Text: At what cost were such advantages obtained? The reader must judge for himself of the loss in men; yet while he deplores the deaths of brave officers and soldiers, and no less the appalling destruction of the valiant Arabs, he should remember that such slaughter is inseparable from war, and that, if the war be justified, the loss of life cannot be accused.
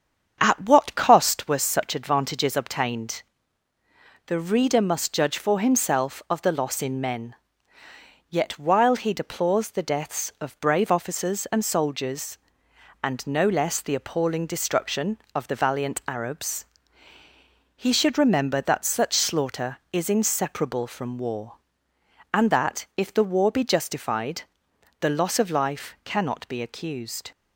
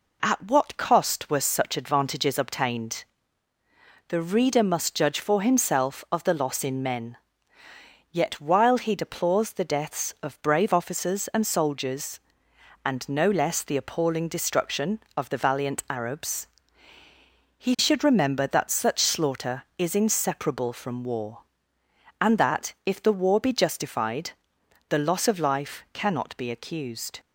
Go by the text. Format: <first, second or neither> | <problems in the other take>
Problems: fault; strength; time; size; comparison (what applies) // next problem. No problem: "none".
second | starts louder than the rest; strong; until 1.5 s; 7.5 dB